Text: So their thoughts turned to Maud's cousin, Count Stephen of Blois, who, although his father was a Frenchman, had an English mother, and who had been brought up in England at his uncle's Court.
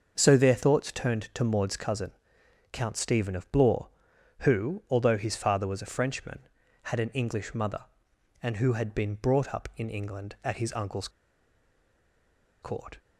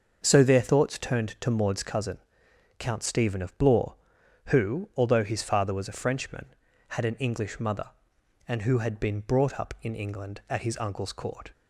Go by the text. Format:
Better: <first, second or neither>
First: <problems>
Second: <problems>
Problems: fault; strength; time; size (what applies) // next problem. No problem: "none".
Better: second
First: starts louder than the rest; until 1.1 s; 6.5 dB // pauses between "uncle's" and "Court"; strong; at 11.0 s; 1.5 s long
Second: starts louder than the rest; until 1.2 s; 6.5 dB